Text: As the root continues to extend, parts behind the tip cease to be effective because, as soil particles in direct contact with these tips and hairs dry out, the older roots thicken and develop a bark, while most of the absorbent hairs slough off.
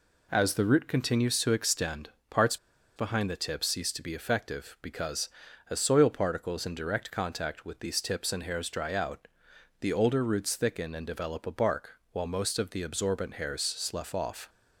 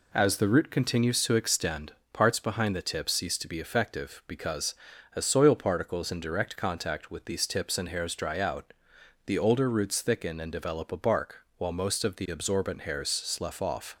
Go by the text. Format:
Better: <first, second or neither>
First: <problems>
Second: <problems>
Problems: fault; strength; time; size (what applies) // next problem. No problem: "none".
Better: second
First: pauses between "parts" and "behind"; at 2.5 s; 0.40 s long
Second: none